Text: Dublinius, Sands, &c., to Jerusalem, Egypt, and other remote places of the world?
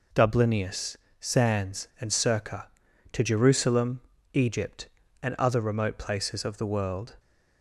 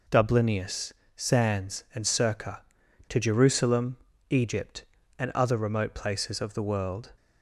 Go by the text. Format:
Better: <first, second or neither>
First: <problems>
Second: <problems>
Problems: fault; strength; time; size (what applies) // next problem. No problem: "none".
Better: neither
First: none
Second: none